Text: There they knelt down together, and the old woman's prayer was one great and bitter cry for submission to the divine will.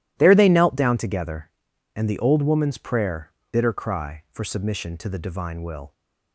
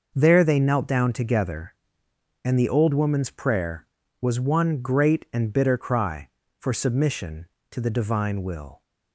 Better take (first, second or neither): second